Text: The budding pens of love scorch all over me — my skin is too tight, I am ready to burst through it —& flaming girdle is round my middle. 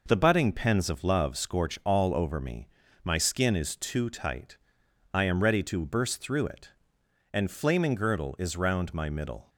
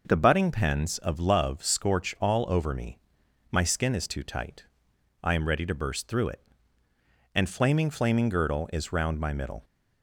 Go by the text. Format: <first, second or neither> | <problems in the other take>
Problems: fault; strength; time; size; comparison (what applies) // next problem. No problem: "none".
first | says "flaming" twice; at 7.8 s